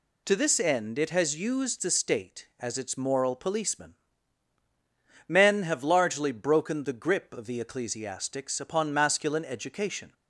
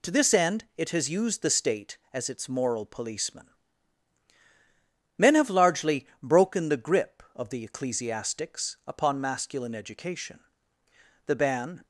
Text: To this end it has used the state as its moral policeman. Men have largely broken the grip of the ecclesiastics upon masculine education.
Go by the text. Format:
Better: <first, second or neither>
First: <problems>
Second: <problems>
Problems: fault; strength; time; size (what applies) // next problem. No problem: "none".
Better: first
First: none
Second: pauses between "largely" and "broken"; slight; at 6.0 s; 0.16 s long // goes on to say "The ban"; from 11.2 s on; 0.58 s long